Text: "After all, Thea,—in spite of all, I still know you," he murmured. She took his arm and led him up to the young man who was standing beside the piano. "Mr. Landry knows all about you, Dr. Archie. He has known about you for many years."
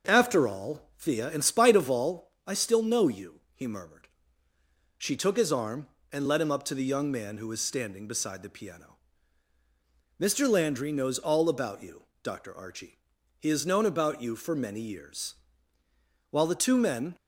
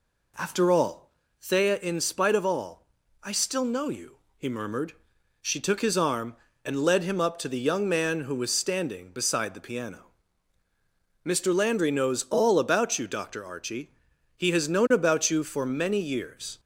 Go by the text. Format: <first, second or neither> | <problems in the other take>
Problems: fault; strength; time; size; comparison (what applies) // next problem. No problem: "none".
second | starts louder than the rest; until 1.1 s; 6 dB // goes on to say "While the two men"; noticeable; from 16.3 s on; 0.84 s long